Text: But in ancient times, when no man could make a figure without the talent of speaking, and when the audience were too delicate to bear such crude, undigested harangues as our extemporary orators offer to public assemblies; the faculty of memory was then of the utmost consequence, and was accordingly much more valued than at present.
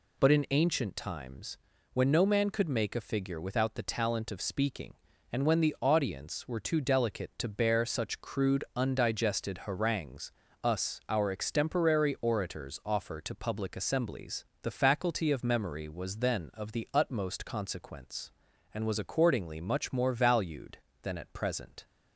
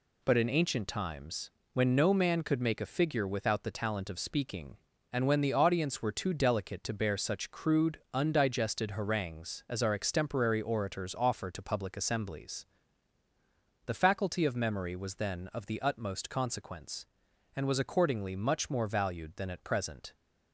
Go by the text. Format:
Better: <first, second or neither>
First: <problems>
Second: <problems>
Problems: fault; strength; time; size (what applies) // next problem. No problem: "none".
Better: second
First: says "us" for "as"; at 10.6 s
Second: none